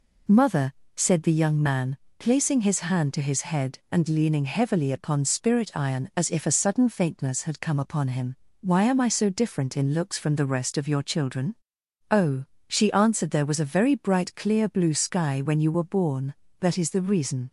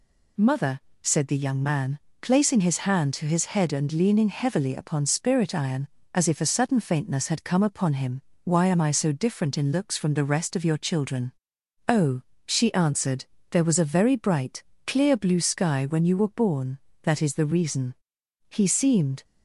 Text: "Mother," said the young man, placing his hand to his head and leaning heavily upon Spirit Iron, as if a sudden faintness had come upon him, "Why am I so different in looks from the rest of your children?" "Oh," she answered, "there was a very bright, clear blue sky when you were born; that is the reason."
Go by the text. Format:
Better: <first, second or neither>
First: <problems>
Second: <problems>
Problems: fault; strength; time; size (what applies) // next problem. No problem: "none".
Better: first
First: none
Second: goes on to say "He seemed"; noticeable; from 18.4 s on; 0.76 s long